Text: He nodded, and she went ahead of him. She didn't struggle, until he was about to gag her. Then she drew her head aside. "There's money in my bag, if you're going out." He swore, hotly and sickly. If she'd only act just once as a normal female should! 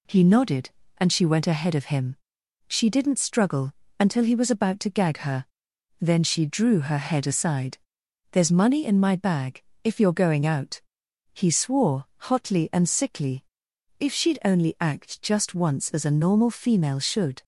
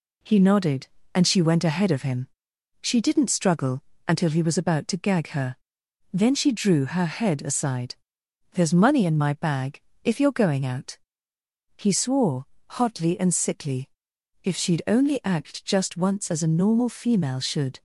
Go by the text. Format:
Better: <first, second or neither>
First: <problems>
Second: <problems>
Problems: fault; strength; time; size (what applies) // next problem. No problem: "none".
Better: neither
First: none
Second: none